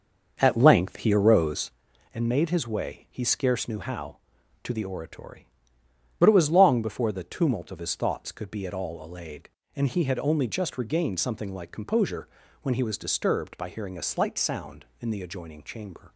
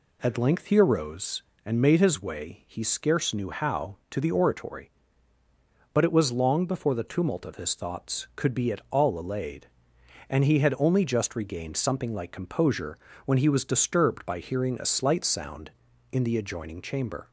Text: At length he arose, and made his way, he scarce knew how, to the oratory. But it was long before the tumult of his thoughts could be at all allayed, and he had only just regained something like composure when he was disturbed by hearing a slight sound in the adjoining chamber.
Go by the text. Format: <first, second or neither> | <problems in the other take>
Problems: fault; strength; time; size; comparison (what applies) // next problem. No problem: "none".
second | starts louder than the rest; until 1.8 s; 6 dB // pauses between "composure" and "when"; slight; at 12.2 s; 0.36 s long; slight in the second